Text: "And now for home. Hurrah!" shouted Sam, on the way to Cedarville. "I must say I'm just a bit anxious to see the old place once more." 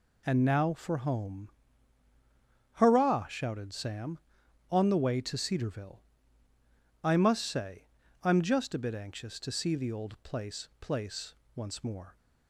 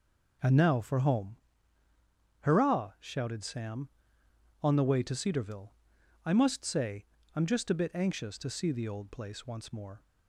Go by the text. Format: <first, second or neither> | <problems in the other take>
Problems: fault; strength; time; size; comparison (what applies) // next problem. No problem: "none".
second | pauses between "say" and "I'm"; slight; at 7.8 s; 0.36 s long; slight in the second // says "place" twice; at 10.8 s